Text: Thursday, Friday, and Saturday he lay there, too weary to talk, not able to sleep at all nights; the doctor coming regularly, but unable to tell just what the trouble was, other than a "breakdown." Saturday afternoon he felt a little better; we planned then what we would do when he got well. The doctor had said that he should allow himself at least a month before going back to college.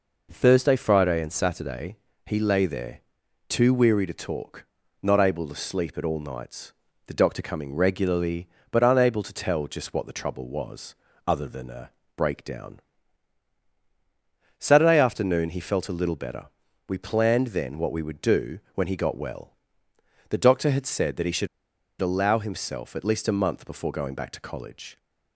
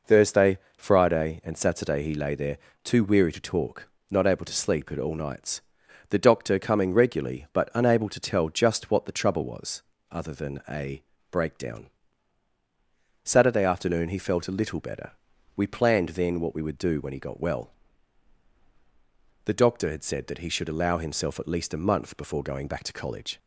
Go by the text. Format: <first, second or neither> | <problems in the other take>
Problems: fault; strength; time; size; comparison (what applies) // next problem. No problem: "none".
second | pauses between "Saturday" and "he"; slight; at 1.9 s; 0.28 s long // pauses between "a" and "breakdown"; slight; at 11.8 s; 0.26 s long; slight in the second // pauses between "do" and "when"; slight; at 18.5 s; 0.16 s long // pauses between "should" and "allow"; noticeable; at 21.4 s; 0.53 s long